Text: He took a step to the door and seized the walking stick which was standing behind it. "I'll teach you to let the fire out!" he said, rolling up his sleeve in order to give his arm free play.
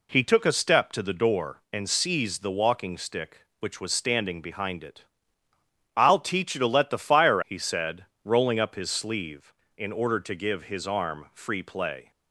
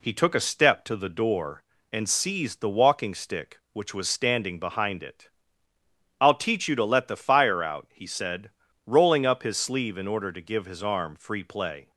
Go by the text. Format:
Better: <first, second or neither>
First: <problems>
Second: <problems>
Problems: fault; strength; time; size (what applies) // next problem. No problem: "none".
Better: second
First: skips "out"; at 7.4 s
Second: none